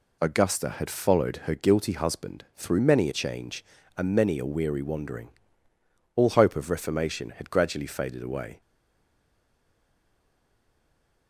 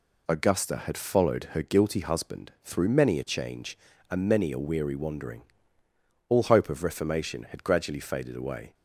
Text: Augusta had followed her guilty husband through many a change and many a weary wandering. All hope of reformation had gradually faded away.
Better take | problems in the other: second | stays silent after the last word; strong; from 8.6 s on; 2.6 s long

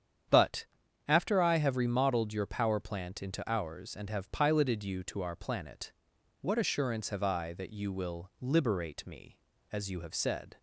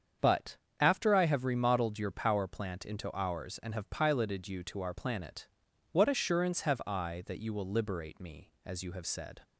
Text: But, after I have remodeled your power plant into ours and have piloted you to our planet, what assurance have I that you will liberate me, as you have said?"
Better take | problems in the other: neither | starts louder than the rest; strong; the same in both

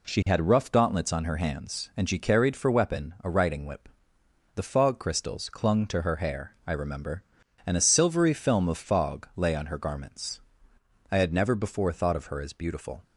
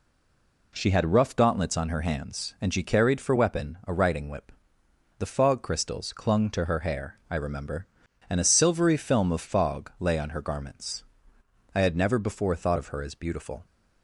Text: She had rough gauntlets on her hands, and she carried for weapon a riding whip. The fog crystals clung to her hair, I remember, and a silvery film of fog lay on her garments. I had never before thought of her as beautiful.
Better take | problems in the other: first | stays silent before the first word; slight; until 0.7 s; 0.7 s long

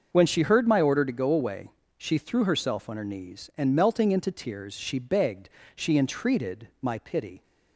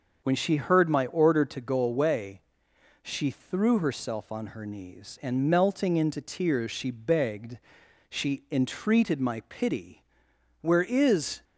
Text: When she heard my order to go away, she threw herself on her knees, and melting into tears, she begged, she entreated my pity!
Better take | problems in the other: first | starts louder than the rest; until 1.2 s; 6.5 dB; also in the first // goes on to say "Where is"; noticeable; from 10.6 s on; 0.82 s long

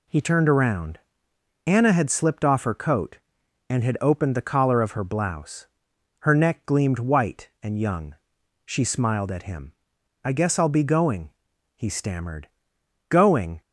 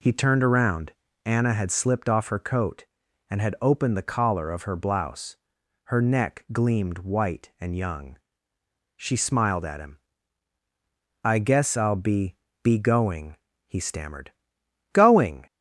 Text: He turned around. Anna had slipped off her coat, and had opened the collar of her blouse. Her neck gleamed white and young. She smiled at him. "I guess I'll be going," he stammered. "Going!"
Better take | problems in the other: first | says "be" twice; at 12.6 s

